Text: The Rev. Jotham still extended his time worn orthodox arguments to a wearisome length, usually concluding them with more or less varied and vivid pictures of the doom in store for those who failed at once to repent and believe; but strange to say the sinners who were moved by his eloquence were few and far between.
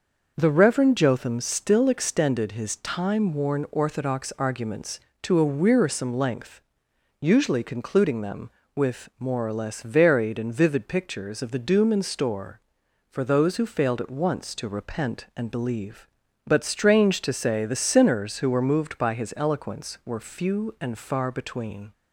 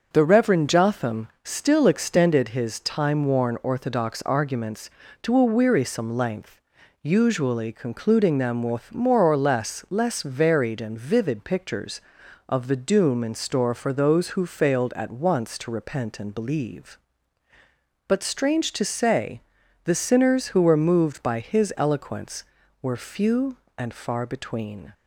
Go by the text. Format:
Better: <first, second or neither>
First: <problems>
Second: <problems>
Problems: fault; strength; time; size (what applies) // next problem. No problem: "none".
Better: first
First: starts louder than the rest; noticeable; until 1.3 s; 6 dB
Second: starts louder than the rest; until 1.1 s; 6.5 dB // pauses between "Jotham" and "still"; slight; at 1.2 s; 0.16 s long // says "less" twice; at 9.8 s // pauses between "say" and "the"; noticeable; at 19.3 s; 0.46 s long